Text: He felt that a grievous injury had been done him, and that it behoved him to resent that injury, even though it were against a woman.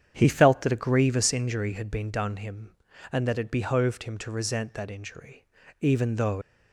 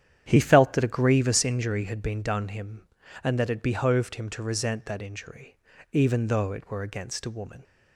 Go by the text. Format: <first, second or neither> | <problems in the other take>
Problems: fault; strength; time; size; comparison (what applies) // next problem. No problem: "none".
second | starts louder than the rest; strong; until 1.1 s; 8.5 dB; strong in the second // stops before "it were against a woman"; at 6.4 s